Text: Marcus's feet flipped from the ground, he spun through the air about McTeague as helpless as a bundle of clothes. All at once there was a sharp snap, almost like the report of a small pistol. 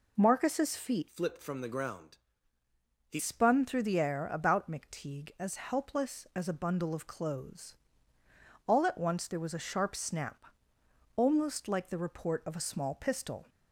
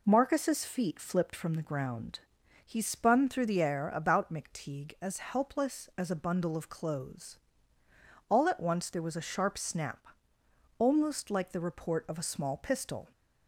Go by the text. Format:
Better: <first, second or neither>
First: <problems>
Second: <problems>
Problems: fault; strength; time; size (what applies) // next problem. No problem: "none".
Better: second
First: changes voice from "flipped" to "he"; from 1.0 to 3.1 s; 2.1 s long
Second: none